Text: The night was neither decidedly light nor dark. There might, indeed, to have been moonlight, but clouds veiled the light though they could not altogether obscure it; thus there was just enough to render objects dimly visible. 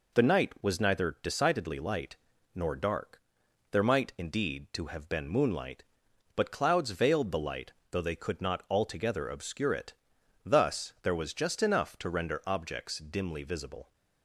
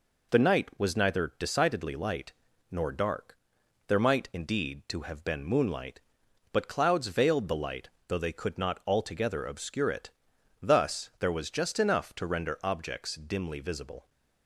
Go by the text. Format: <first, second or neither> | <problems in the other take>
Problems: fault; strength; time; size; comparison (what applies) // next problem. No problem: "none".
neither | pauses between "light" and "nor"; slight; the same in both // pauses between "light" and "though"; slight; the same in both